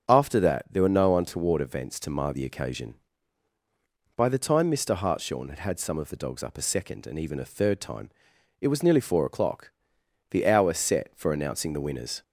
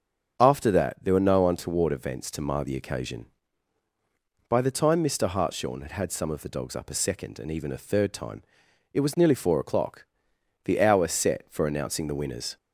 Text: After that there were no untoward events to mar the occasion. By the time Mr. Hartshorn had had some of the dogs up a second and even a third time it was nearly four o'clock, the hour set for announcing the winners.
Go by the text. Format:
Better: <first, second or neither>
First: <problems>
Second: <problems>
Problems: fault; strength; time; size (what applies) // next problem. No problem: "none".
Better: neither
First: starts louder than the rest; strong; until 1.1 s; 7.5 dB // pauses between "time" and "it"; noticeable; at 8.1 s; 0.50 s long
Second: starts louder than the rest; strong; until 1.4 s; 7.5 dB // pauses between "time" and "it"; noticeable; at 8.4 s; 0.50 s long